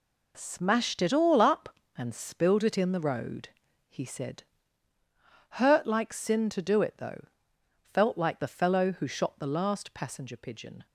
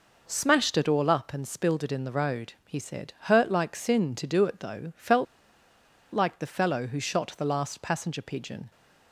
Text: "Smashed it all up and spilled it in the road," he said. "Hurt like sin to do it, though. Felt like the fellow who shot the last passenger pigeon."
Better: first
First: none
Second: pauses between "Felt" and "like"; noticeable; at 5.2 s; 0.89 s long

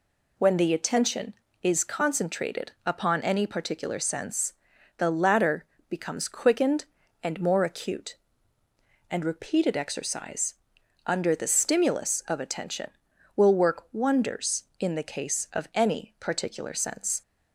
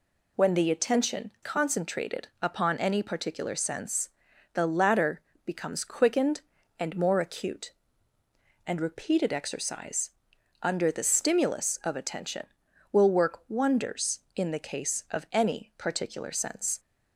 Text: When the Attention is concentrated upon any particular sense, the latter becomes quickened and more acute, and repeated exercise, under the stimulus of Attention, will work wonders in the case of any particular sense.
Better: first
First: pauses between "latter" and "becomes"; slight; at 5.6 s; 0.24 s long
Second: skips "is"; at 1.3 s // pauses between "latter" and "becomes"; slight; at 5.2 s; 0.24 s long

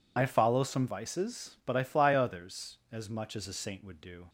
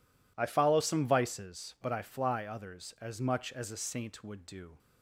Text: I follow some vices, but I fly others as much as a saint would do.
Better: second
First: loses the start of "I"; at 0.1 s; 45 ms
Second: none

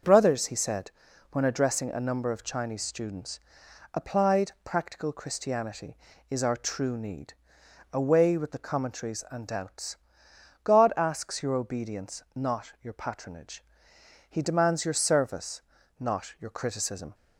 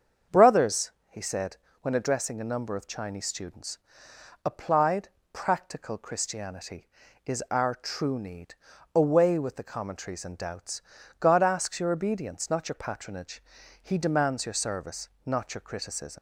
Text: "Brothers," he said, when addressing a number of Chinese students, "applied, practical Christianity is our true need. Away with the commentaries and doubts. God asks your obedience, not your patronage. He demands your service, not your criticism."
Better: first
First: starts louder than the rest; until 1.4 s; 6.5 dB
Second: starts louder than the rest; until 1.4 s; 7 dB // leaves "criticism" unfinished; at 16.1 s; 95 ms

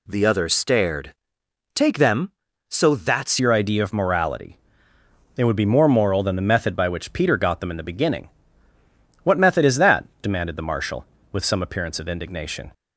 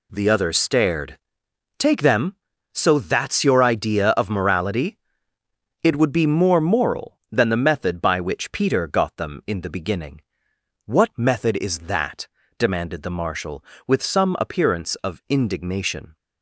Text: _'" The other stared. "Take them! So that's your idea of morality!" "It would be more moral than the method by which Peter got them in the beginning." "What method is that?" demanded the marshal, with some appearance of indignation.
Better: second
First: changes voice at "your"; from 3.3 s on; 9.4 s long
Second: none

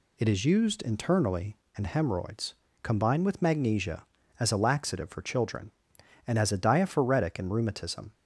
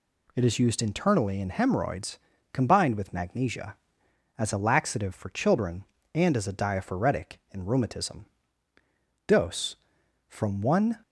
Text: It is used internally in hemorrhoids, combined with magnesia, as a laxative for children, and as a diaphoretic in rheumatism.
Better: first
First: none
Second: goes on to say "Dose from one"; strong; from 9.2 s on; 1.7 s long

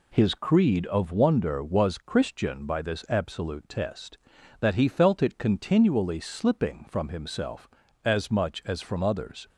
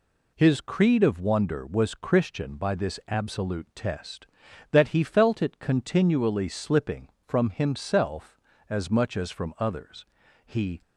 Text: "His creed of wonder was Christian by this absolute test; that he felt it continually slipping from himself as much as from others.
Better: first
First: none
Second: goes on to say "He"; slight; from 10.4 s on; 0.38 s long

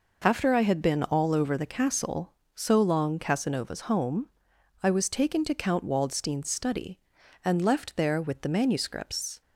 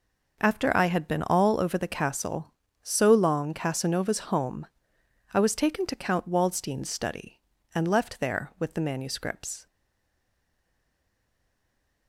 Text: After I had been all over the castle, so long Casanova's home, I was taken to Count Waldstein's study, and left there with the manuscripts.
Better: first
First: none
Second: stays silent after the last word; from 9.6 s on; 2.4 s long

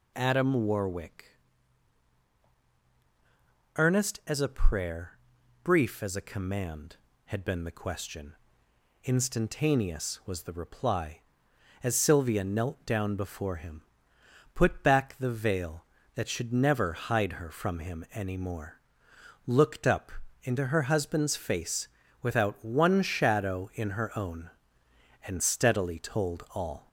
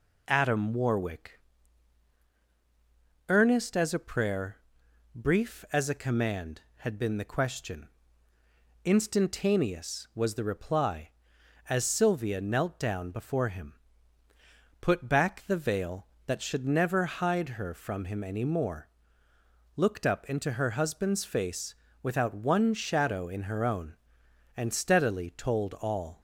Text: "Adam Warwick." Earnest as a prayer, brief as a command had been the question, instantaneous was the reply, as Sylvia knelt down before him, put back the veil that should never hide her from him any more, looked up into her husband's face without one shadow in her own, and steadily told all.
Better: second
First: gets louder; slight; throughout; 3 dB // pauses between "up" and "into"; slight; at 20.1 s; 0.32 s long // pauses between "face" and "without"; slight; at 21.8 s; 0.34 s long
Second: pauses between "face" and "without"; slight; at 21.7 s; 0.28 s long

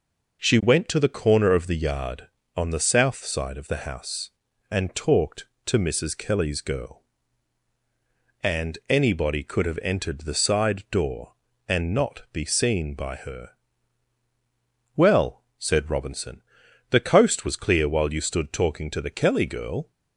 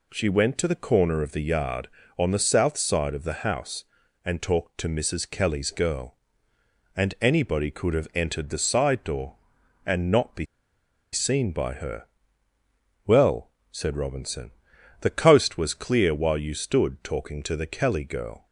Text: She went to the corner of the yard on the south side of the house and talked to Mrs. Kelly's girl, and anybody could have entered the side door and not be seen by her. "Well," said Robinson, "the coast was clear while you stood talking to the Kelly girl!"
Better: first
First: none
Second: pauses between "be" and "seen"; noticeable; at 10.4 s; 0.67 s long

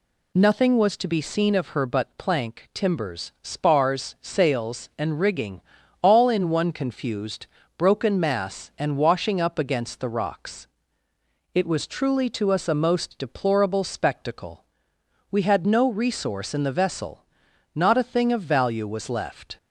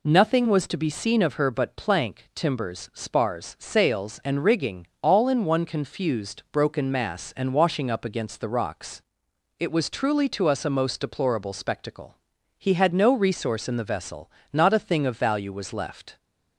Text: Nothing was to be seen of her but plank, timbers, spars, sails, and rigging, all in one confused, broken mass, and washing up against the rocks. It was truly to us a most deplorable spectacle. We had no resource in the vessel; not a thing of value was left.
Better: first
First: none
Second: says "He" for "We"; at 12.5 s

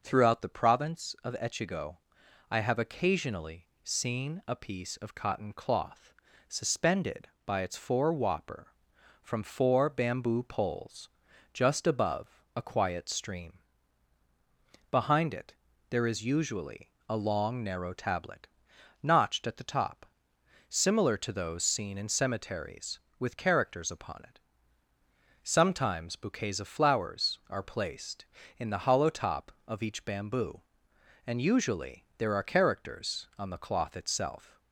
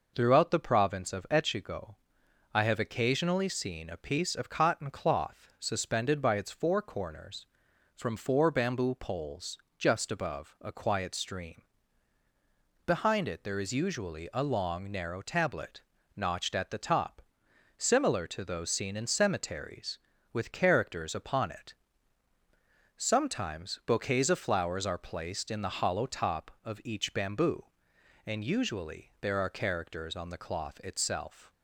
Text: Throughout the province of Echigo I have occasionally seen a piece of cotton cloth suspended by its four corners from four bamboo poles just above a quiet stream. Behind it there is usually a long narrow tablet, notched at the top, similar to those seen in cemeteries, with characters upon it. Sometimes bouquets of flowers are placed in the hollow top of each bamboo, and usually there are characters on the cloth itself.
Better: second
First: pauses between "Echigo" and "I"; noticeable; at 1.9 s; 0.54 s long // pauses between "occasionally" and "seen"; slight; at 3.6 s; 0.16 s long // pauses between "cloth" and "suspended"; slight; at 6.1 s; 0.36 s long // says "whopper" for "corners"; at 8.1 s // pauses between "poles" and "just"; at 11.0 s; 0.44 s long // pauses between "it" and "there"; slight; at 15.5 s; 0.34 s long // pauses between "usually" and "a"; slight; at 16.8 s; 0.20 s long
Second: pauses between "Echigo" and "I"; noticeable; at 1.9 s; 0.58 s long // pauses between "poles" and "just"; slight; at 9.5 s; 0.22 s long

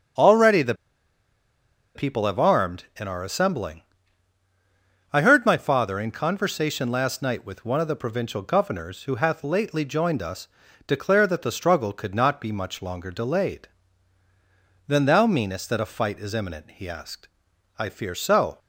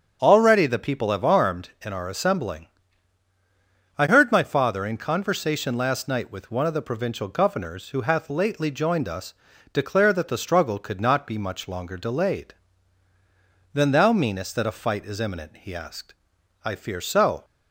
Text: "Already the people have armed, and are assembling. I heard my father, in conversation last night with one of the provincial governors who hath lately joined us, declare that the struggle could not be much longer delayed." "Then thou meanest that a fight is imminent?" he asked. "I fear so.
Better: second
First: starts louder than the rest; strong; until 2.4 s; 7 dB // pauses between "the" and "people"; at 0.7 s; 1.2 s long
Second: starts louder than the rest; strong; until 1.2 s; 7 dB

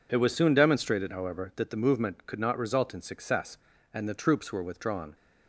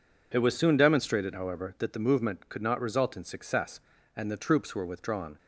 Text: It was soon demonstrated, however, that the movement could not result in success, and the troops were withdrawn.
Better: neither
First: none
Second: none

